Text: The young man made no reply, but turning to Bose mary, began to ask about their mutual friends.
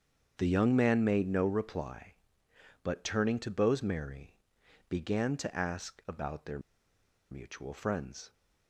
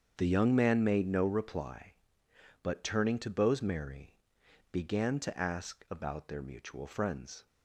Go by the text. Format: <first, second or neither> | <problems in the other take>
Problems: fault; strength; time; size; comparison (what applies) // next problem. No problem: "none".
second | starts louder than the rest; strong; until 1.3 s; 7.5 dB; strong in the second // pauses between "their" and "mutual"; noticeable; at 6.5 s; 0.72 s long